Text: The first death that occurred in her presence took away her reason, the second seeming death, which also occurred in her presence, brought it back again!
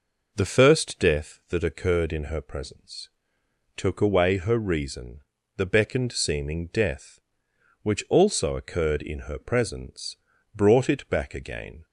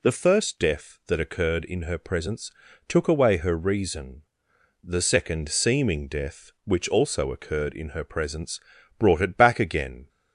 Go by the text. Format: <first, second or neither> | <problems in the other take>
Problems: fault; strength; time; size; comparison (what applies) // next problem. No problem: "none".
second | pauses between "presence" and "took"; noticeable; at 3.0 s; 0.68 s long; slight in the second // says "beckoned" for "second"; at 5.6 s